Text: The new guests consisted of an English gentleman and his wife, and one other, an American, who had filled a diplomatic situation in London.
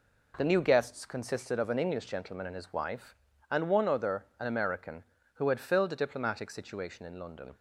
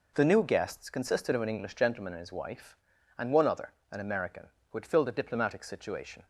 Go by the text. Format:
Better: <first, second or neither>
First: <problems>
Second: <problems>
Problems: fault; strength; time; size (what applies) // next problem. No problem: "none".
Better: first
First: none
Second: stops before "in London"; at 6.2 s